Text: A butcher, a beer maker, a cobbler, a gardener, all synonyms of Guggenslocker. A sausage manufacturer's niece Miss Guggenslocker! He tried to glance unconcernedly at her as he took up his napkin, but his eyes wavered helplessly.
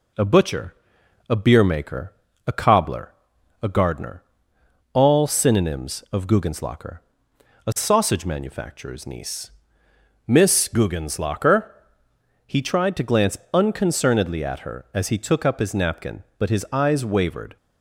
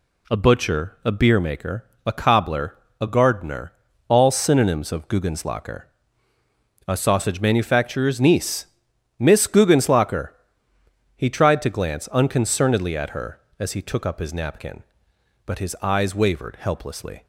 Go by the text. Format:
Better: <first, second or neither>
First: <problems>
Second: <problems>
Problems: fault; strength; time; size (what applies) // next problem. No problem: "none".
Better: second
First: pauses between "niece" and "Miss"; noticeable; at 9.5 s; 0.76 s long // pauses between "glance" and "unconcernedly"; slight; at 13.3 s; 0.16 s long // stops before "helplessly"; at 17.5 s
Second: pauses between "niece" and "Miss"; noticeable; at 8.6 s; 0.54 s long